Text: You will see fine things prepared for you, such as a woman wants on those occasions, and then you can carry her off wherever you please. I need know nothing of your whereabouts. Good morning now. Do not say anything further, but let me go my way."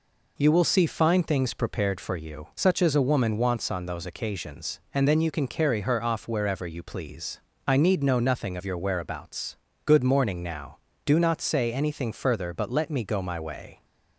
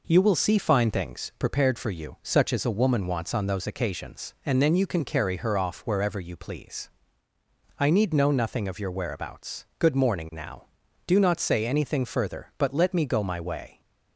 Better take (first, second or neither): neither